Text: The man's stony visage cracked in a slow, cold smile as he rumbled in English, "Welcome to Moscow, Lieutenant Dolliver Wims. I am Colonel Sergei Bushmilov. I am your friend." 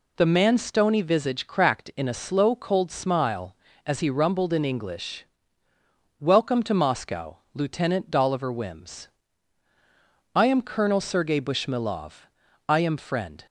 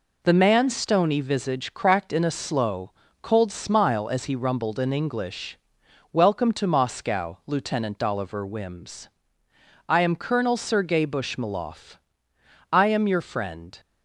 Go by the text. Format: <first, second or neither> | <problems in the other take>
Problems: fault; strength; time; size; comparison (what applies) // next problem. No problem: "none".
second | skips "your"; at 12.9 s